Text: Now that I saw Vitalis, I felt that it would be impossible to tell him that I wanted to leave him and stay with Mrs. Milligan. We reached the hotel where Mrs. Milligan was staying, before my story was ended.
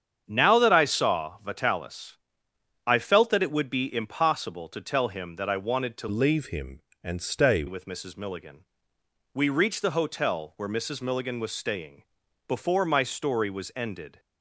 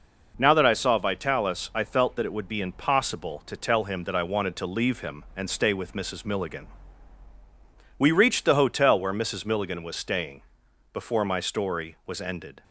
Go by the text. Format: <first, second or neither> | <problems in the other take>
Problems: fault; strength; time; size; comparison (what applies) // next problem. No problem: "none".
second | starts louder than the rest; strong; until 1.2 s; 8 dB // changes voice from "leave" to "stay"; from 6.0 to 7.6 s; 1.6 s long